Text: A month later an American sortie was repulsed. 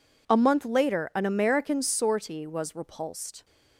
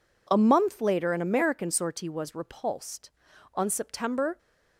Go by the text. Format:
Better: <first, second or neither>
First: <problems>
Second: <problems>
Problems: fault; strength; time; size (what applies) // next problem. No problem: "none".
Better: first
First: none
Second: goes on to say "On September"; noticeable; from 3.5 s on; 0.84 s long